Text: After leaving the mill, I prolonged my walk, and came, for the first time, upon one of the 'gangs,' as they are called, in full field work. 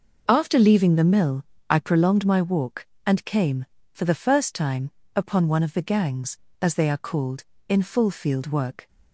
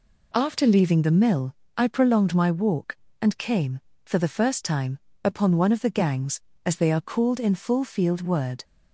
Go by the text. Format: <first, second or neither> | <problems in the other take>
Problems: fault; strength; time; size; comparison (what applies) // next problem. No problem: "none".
first | says "word" for "work"; at 8.2 s